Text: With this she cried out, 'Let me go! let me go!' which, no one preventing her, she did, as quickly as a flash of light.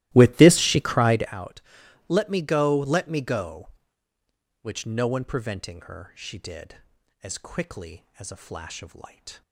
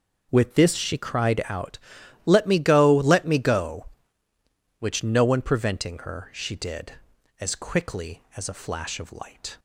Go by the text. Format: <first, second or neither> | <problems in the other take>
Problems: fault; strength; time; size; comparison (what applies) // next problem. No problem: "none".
second | starts louder than the rest; strong; until 1.4 s; 16 dB